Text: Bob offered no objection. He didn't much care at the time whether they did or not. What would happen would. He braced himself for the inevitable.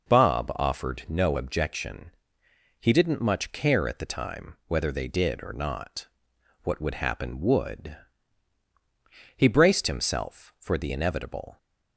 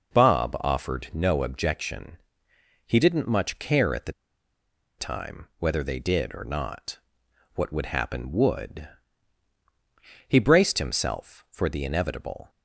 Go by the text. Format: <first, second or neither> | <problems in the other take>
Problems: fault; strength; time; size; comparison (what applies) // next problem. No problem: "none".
first | pauses between "the" and "time"; noticeable; at 4.1 s; 0.87 s long